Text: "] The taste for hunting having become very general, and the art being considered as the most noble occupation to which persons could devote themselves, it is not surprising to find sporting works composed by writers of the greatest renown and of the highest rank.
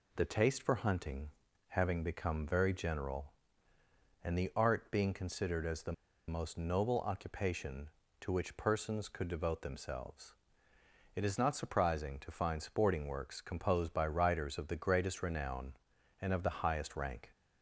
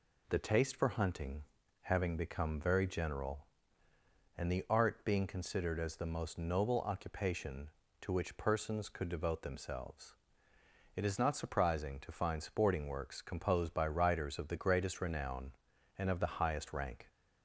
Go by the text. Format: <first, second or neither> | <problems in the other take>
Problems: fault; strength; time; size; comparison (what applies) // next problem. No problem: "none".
second | pauses between "hunting" and "having"; at 1.2 s; 0.38 s long; also in the second // pauses between "the" and "most"; slight; at 5.9 s; 0.35 s long